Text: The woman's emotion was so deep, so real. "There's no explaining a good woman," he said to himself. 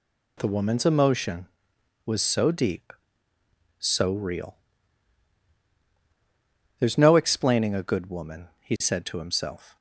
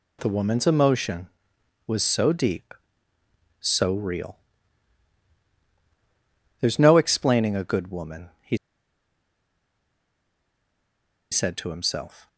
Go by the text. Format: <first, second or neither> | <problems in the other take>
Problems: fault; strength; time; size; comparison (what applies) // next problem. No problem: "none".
first | pauses between "he" and "said"; strong; at 8.5 s; 2.7 s long